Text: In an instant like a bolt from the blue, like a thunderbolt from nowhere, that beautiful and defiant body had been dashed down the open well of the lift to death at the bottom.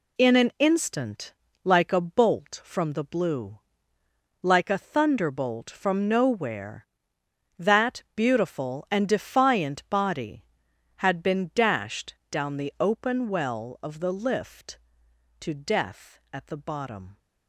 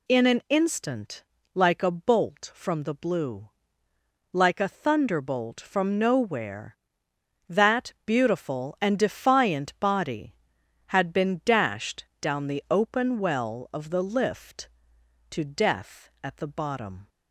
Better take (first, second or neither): second